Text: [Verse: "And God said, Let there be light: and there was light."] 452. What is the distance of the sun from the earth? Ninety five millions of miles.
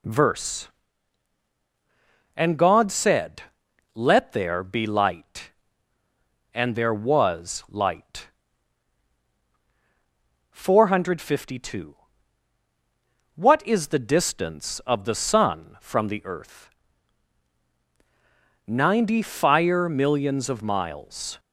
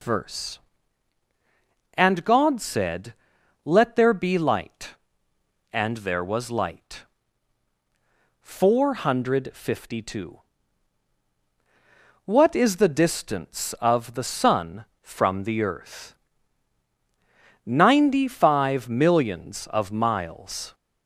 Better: second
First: says "fire" for "five"; at 19.2 s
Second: none

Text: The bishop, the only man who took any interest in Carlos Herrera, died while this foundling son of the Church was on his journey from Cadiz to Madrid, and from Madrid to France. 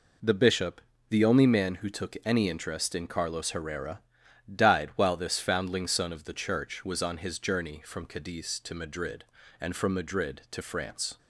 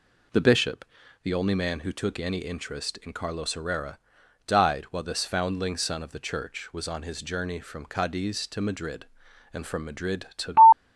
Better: first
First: none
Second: stops before "France"; at 10.7 s

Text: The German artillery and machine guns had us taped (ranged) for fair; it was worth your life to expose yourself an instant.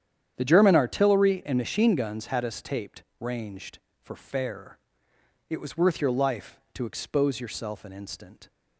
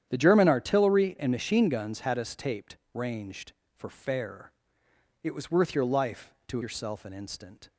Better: first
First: starts louder than the rest; strong; until 1.3 s; 9.5 dB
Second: starts louder than the rest; strong; until 1.1 s; 10 dB // skips "expose"; at 6.6 s

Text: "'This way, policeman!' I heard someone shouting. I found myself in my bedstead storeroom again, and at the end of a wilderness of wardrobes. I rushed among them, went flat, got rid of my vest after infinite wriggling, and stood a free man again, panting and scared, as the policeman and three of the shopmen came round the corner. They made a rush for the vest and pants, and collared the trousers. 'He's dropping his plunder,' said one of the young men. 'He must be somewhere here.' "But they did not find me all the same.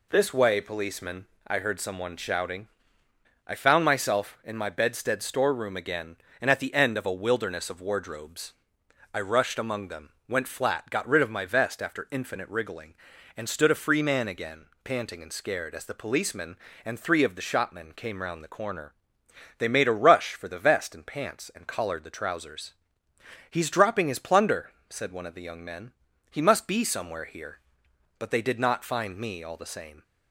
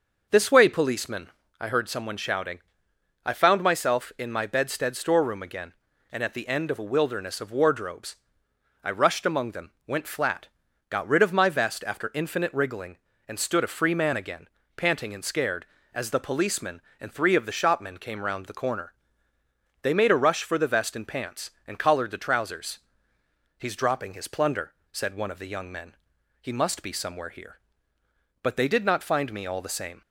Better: neither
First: none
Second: none

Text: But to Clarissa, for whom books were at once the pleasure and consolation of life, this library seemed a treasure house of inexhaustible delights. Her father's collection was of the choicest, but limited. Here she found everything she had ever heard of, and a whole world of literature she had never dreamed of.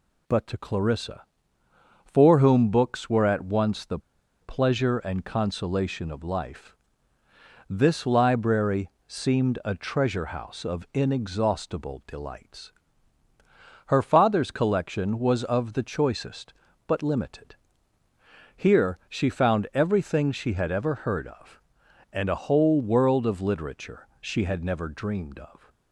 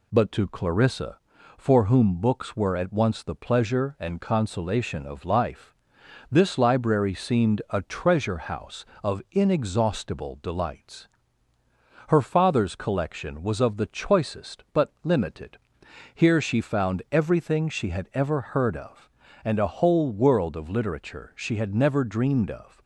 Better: second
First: pauses between "the" and "pleasure"; at 3.9 s; 0.42 s long // pauses between "library" and "seemed"; slight; at 8.8 s; 0.16 s long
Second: none

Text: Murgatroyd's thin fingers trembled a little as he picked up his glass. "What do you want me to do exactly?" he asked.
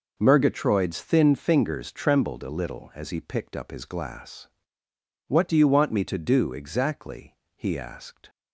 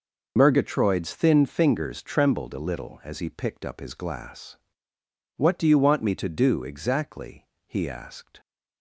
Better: first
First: none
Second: loses the start of "Murgatroyd's"; at 0.3 s; 45 ms

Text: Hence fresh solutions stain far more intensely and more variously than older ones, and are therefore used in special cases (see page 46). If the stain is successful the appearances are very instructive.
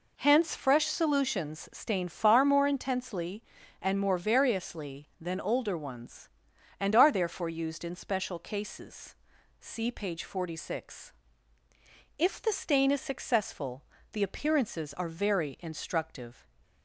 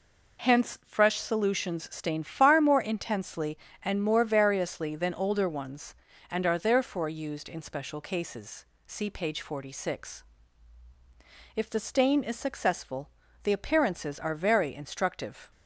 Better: neither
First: pauses between "successful" and "the"; slight; at 13.8 s; 0.30 s long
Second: pauses between "successful" and "the"; slight; at 13.1 s; 0.32 s long

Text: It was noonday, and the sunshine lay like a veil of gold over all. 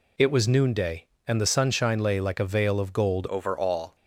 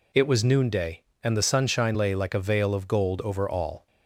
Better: second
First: changes voice at "over"; from 3.2 s on; 0.7 s long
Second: none

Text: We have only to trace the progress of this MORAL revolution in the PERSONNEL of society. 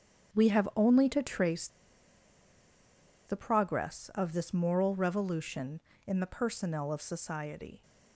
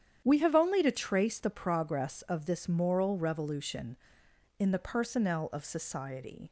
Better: second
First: starts louder than the rest; strong; until 1.4 s; 8 dB // pauses between "trace" and "the"; strong; at 1.6 s; 1.5 s long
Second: starts louder than the rest; strong; until 1.2 s; 9.5 dB

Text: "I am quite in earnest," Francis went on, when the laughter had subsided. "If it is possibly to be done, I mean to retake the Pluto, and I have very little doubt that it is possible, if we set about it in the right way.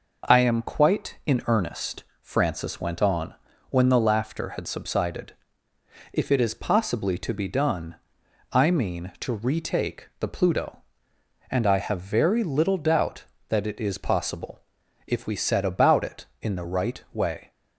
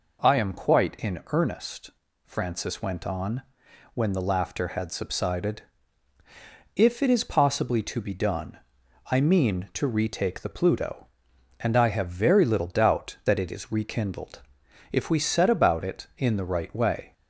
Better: first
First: none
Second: says "rekindled" for "possible"; at 13.7 s

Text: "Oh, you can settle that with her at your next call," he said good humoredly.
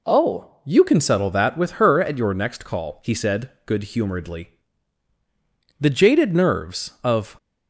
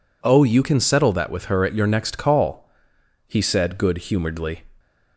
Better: second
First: goes on to say "The jaded nerves of"; from 5.7 s on; 1.5 s long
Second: none

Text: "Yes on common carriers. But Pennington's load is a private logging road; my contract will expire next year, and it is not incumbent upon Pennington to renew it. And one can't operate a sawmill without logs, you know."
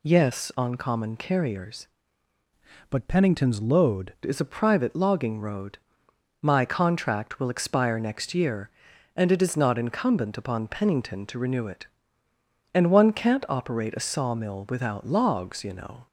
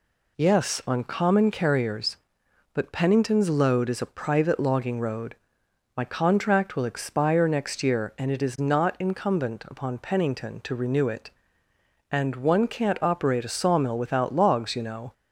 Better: second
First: changes voice from "But" to "load"; from 2.8 to 4.1 s; 1.3 s long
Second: none

